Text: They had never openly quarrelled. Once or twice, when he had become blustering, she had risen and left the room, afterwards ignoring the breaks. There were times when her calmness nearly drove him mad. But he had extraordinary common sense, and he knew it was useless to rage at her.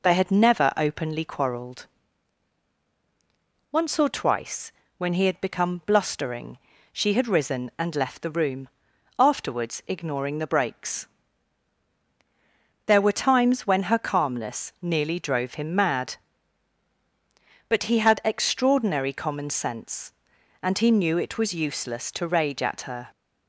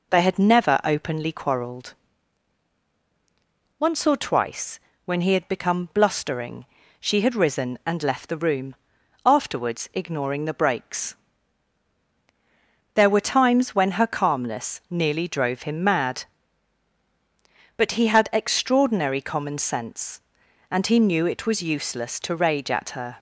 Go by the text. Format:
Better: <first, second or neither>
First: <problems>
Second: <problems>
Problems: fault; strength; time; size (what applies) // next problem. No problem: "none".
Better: neither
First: none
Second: none